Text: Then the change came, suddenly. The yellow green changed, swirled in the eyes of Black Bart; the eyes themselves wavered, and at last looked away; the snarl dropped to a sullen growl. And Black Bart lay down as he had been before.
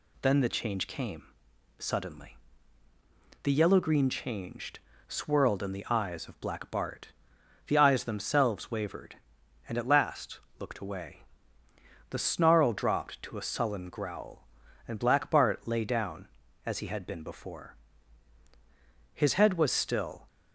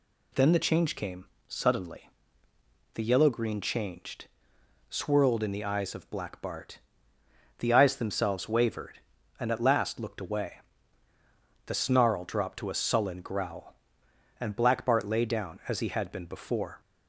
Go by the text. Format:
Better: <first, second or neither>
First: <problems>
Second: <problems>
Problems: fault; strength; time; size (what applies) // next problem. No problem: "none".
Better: second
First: pauses between "last" and "looked"; slight; at 10.3 s; 0.18 s long // goes on to say "His head was still"; noticeable; from 19.1 s on; 1.1 s long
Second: none